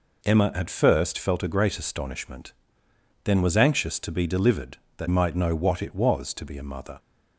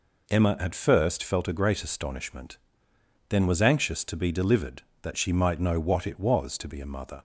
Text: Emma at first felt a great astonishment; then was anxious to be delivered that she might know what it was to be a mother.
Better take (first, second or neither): second